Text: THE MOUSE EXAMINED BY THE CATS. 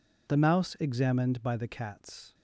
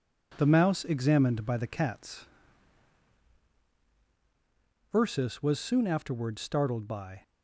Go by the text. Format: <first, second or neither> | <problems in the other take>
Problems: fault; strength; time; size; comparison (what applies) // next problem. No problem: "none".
first | goes on to say "Ursus was soon afterwards startled by"; strong; from 4.9 s on; 2.2 s long